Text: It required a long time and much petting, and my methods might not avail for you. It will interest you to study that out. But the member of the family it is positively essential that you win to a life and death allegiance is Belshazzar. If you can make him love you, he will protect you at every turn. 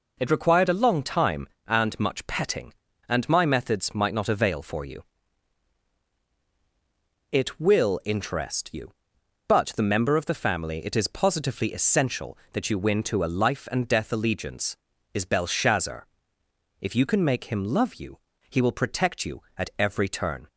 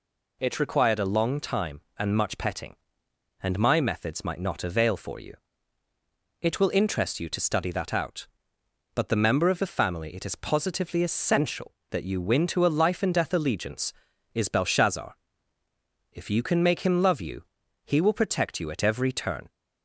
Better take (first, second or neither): second